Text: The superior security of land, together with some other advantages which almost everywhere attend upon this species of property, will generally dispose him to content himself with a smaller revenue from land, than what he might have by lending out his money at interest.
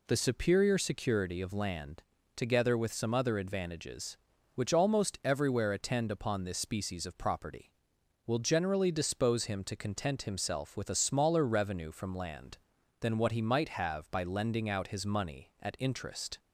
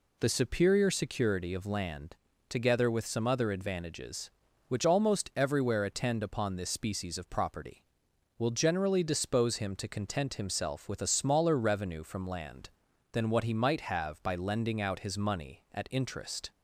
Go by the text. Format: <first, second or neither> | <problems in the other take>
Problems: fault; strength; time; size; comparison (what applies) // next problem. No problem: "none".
neither | none